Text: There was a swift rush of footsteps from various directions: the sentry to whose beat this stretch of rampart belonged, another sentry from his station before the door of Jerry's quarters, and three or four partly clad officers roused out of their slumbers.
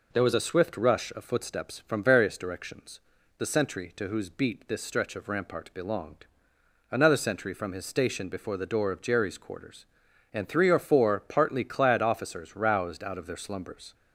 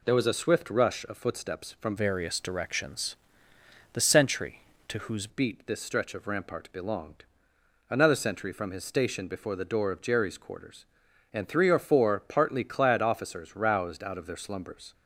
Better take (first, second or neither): first